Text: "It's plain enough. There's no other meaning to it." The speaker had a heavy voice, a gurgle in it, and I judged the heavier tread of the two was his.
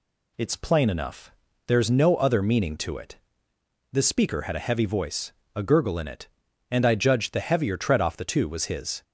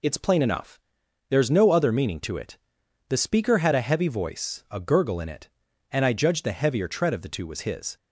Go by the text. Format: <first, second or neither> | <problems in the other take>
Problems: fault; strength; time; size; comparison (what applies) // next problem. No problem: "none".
second | says "off" for "of"; at 8.0 s